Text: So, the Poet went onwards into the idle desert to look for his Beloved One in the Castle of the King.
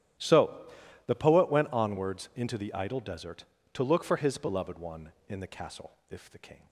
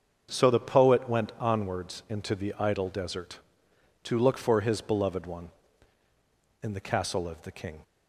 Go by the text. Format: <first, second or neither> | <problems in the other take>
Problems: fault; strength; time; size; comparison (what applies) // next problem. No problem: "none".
second | starts louder than the rest; strong; until 1.5 s; 11.5 dB; also in the second // says "if" for "of"; at 6.0 s